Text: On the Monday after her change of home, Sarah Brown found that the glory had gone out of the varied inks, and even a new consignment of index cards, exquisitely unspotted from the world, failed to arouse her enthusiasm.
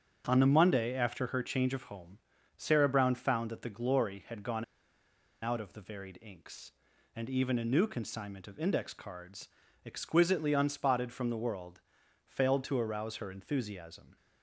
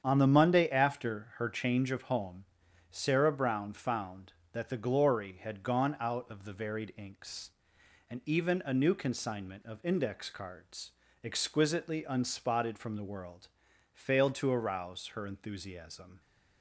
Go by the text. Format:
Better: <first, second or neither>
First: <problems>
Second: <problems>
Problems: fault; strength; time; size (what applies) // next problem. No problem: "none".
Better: second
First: starts louder than the rest; until 1.3 s; 7 dB // pauses between "gone" and "out"; noticeable; at 4.6 s; 0.78 s long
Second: starts louder than the rest; strong; until 1.0 s; 8 dB